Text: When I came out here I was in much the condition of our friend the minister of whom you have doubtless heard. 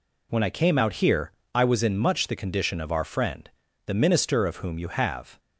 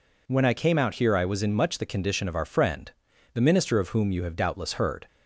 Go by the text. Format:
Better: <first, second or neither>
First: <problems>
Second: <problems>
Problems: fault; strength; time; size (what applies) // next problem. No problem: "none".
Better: second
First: pauses between "here" and "I"; slight; at 1.3 s; 0.24 s long // pauses between "friend" and "the"; at 3.4 s; 0.38 s long // stops before "doubtless heard"; at 5.3 s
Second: pauses between "friend" and "the"; at 2.9 s; 0.44 s long